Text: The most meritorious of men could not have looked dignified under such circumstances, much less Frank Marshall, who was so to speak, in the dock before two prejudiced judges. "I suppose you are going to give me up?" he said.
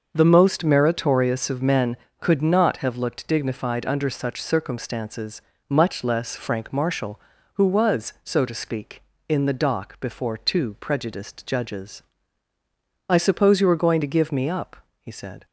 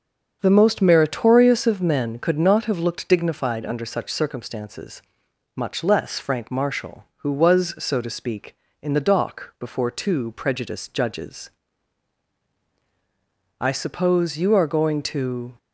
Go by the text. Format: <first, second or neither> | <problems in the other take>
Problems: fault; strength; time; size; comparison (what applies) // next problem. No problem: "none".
first | starts louder than the rest; until 1.4 s; 7 dB; also in the first // stops before "give me up he said"; at 15.5 s